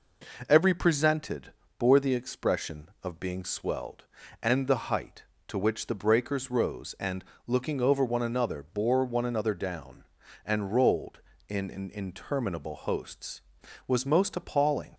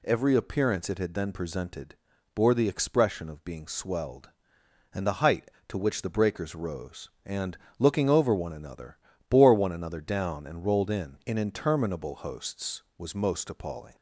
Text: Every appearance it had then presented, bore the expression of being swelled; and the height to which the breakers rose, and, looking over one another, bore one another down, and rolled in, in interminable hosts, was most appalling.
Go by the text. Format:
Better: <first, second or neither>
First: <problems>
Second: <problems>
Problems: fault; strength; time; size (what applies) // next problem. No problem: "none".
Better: second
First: skips "appearance it had then"; at 0.7 s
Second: none